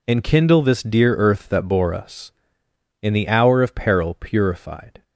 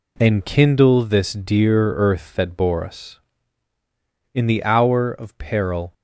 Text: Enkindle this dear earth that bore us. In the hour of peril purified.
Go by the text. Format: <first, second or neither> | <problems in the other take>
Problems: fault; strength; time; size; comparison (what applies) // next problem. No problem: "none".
first | stops before "purified"; at 5.9 s